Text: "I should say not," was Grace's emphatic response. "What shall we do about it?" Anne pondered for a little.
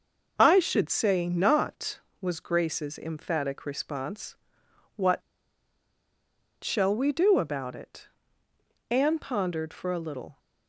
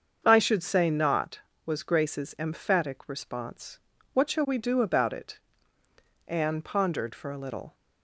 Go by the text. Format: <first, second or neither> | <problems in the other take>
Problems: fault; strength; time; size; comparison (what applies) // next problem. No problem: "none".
second | starts louder than the rest; noticeable; until 1.3 s; 6 dB; also in the second // pauses between "What" and "shall"; strong; at 5.2 s; 1.4 s long